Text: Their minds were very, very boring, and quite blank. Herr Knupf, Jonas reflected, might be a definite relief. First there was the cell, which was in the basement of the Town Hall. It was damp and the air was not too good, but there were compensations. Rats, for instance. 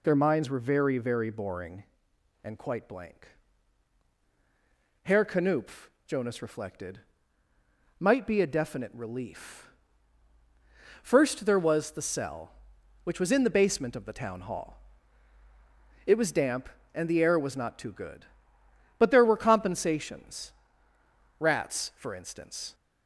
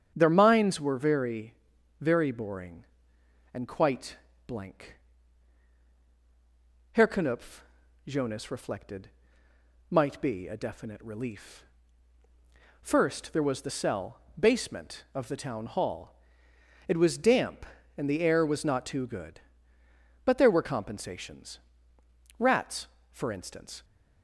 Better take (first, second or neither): first